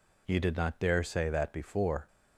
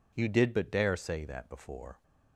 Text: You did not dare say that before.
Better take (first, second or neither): first